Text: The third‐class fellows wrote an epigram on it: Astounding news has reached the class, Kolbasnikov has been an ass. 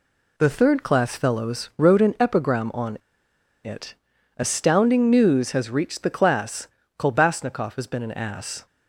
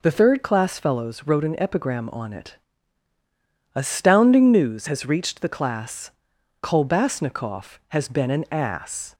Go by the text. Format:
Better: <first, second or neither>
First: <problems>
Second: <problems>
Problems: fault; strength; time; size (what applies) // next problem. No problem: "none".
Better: second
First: pauses between "on" and "it"; noticeable; at 2.9 s; 0.65 s long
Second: none